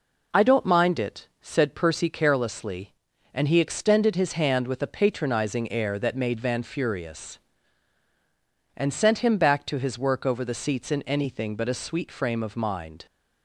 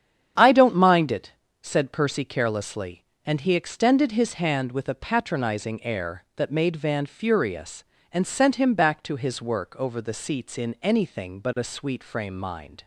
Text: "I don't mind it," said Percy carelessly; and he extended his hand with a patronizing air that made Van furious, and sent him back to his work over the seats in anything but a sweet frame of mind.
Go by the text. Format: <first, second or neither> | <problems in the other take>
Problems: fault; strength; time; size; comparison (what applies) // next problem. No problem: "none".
first | starts louder than the rest; strong; until 1.6 s; 8.5 dB // skips "of"; at 12.3 s